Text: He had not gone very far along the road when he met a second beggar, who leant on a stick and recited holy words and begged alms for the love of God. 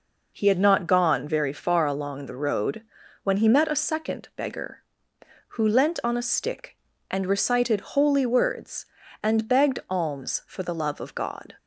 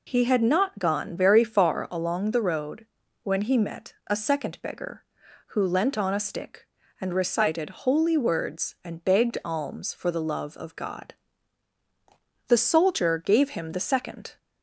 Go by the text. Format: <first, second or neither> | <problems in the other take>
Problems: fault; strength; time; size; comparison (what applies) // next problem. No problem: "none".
first | pauses between "road" and "when"; at 2.8 s; 0.38 s long; also in the first // goes on to say "The soldier gave him the second"; strong; from 12.4 s on; 1.9 s long